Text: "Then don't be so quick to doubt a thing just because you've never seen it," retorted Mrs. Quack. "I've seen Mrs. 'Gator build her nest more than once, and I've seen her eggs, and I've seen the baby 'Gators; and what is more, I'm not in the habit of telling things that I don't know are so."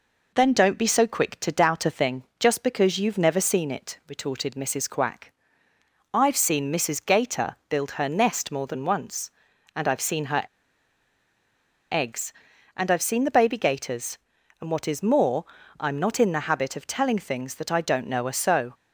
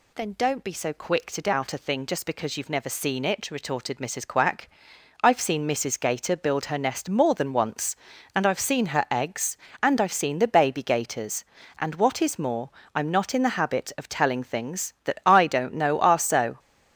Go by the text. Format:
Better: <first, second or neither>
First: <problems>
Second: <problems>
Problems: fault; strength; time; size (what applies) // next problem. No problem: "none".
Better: second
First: pauses between "thing" and "just"; slight; at 2.2 s; 0.16 s long // pauses between "her" and "eggs"; strong; at 10.4 s; 1.4 s long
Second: none